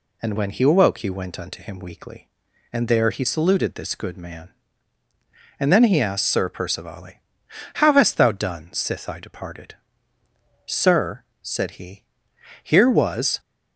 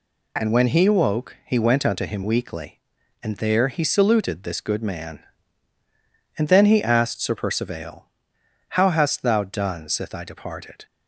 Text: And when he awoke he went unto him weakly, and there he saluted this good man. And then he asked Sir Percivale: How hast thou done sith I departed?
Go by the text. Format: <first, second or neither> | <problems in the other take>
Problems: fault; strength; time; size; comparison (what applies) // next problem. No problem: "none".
second | goes on to say "Sir said he here was"; strong; from 10.6 s on; 2.7 s long